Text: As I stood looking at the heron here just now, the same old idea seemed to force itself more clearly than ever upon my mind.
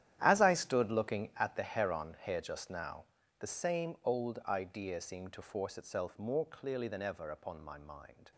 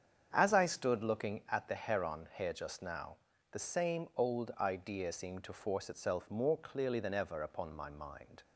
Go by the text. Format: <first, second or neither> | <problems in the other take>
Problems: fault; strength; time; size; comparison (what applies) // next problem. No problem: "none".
second | gets quieter; strong; throughout; 14.5 dB // starts louder than the rest; strong; until 1.2 s; 11.5 dB; strong in the second